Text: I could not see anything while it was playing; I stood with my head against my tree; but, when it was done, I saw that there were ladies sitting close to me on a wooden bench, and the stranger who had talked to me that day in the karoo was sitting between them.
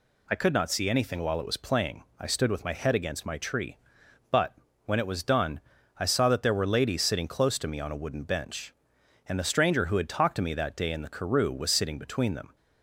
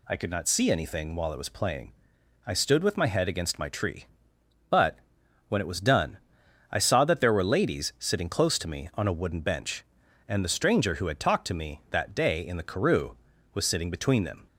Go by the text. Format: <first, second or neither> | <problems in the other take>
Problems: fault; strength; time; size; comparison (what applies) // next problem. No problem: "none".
neither | none